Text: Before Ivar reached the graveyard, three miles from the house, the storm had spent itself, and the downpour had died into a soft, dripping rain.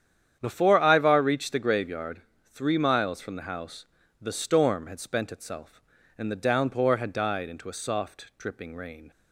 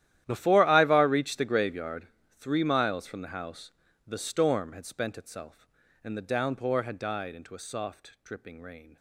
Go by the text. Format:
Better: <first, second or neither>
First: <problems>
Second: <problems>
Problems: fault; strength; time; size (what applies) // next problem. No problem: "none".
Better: first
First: starts louder than the rest; strong; until 1.4 s; 9 dB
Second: gets quieter; strong; throughout; 17.5 dB // starts louder than the rest; strong; until 1.2 s; 12.5 dB